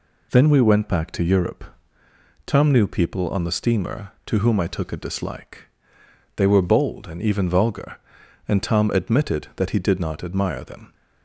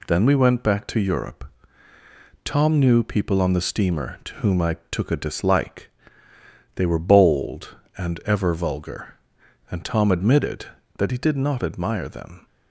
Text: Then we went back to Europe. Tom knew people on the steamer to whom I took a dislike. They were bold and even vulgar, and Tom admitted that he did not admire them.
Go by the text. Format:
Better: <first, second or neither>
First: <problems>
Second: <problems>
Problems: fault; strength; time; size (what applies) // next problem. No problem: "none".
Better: first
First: none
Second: says "ever" for "even"; at 8.2 s